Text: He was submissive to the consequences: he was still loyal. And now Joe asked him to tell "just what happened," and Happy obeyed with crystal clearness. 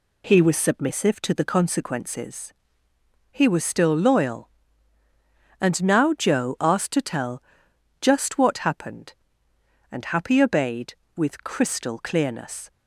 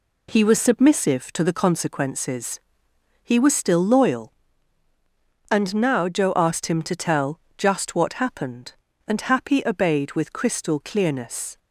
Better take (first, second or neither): second